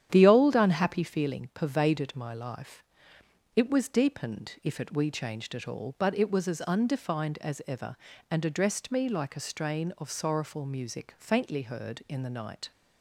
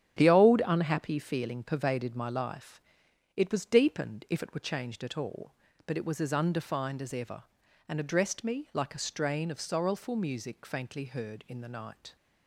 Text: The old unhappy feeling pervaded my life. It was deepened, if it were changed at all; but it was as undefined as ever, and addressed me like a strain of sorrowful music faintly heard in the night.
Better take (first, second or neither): second